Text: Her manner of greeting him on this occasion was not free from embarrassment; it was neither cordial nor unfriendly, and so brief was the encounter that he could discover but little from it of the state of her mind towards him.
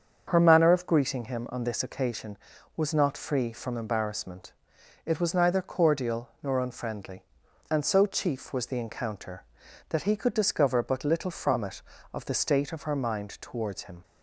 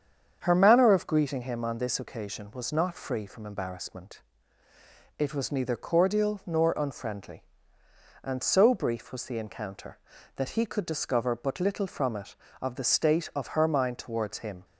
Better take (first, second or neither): second